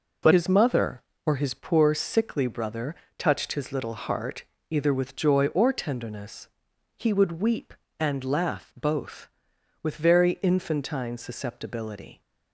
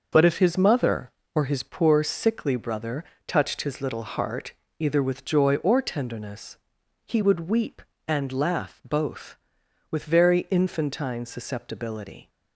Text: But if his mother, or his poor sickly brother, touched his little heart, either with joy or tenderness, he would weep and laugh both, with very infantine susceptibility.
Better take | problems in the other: second | skips "if"; at 0.3 s

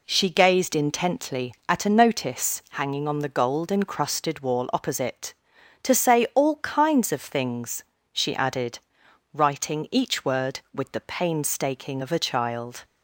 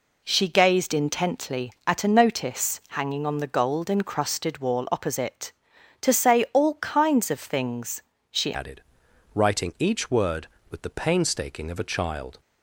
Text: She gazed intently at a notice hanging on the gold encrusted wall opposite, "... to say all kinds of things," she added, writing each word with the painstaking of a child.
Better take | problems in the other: first | changes voice at "added"; from 8.5 s on; 3.9 s long

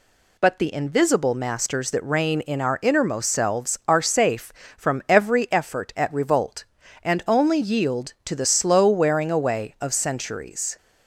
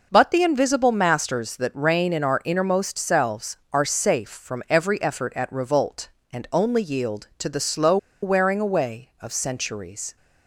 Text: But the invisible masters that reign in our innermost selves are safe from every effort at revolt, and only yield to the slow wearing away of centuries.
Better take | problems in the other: first | pauses between "slow" and "wearing"; slight; at 7.9 s; 0.25 s long

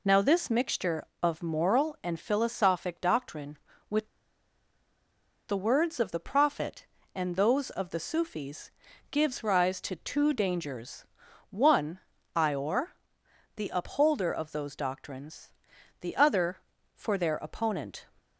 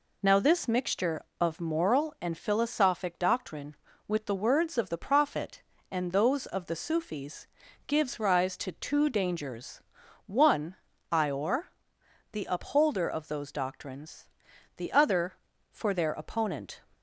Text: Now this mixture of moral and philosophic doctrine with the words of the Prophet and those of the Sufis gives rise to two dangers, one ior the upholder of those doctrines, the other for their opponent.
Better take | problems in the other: second | pauses between "with" and "the"; strong; at 4.0 s; 1.4 s long // pauses between "Sufis" and "gives"; at 8.7 s; 0.40 s long; also in the second // pauses between "one" and "ior"; slight; at 11.9 s; 0.36 s long; slight in the second // pauses between "ior" and "the"; noticeable; at 12.9 s; 0.66 s long; noticeable in the second

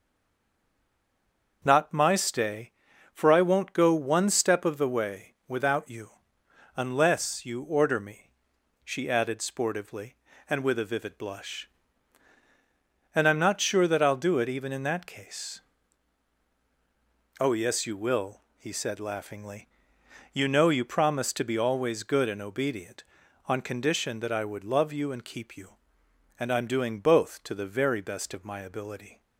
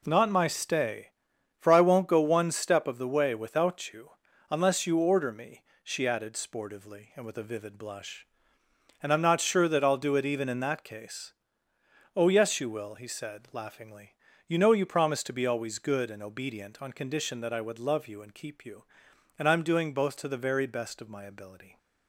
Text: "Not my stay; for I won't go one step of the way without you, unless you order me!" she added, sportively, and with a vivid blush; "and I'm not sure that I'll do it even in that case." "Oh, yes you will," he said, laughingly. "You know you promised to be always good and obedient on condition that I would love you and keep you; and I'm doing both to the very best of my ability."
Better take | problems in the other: second | stays silent before the first word; noticeable; until 1.6 s; 1.6 s long // starts louder than the rest; until 2.6 s; 6.5 dB

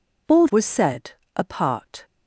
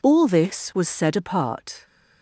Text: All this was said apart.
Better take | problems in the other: second | skips "this"; at 0.4 s // pauses between "said" and "apart"; slight; at 1.1 s; 0.24 s long

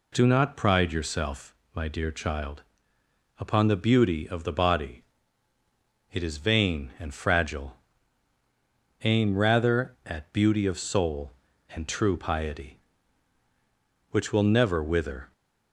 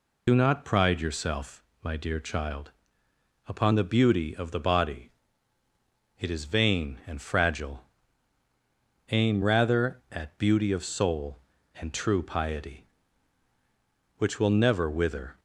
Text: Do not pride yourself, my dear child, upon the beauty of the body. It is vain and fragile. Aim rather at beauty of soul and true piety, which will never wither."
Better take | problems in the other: first | loses the start of "Do"; at 0.2 s; 65 ms

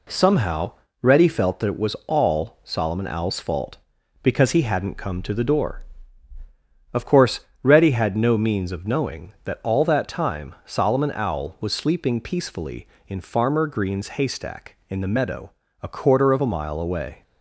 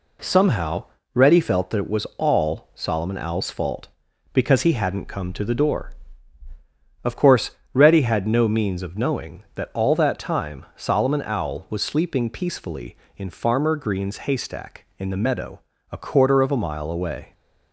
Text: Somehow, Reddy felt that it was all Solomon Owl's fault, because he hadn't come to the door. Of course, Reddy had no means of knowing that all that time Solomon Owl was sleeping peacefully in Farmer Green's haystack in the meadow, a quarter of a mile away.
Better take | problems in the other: neither | none

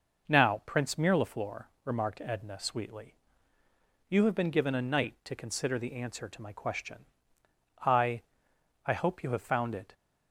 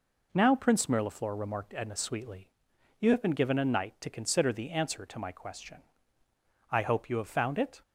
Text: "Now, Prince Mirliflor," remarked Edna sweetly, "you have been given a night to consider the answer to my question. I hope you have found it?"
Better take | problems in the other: second | says "I" twice; at 8.8 s

